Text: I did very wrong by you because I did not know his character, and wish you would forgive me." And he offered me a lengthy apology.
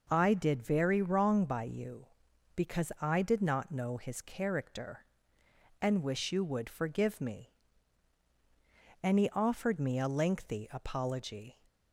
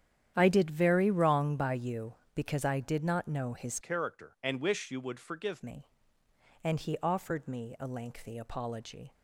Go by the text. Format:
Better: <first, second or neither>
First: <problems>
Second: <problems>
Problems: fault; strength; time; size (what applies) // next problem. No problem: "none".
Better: first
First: none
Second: starts louder than the rest; strong; until 1.3 s; 10 dB // changes voice from "character" to "forgive"; from 3.8 to 5.6 s; 1.8 s long